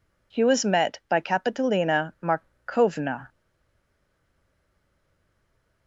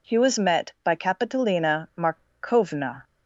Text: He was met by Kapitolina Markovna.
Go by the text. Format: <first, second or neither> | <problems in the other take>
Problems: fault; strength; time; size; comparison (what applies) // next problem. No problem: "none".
second | stays silent after the last word; strong; from 3.2 s on; 2.6 s long